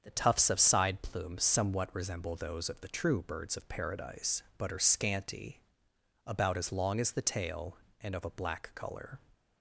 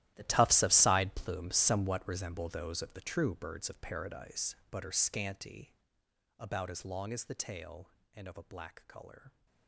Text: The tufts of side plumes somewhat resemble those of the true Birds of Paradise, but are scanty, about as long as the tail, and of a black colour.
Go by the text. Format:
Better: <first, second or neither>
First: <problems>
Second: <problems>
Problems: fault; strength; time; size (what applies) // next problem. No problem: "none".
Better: first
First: starts louder than the rest; strong; until 1.0 s; 7 dB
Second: gets quieter; strong; throughout; 16 dB // starts louder than the rest; strong; until 1.1 s; 13.5 dB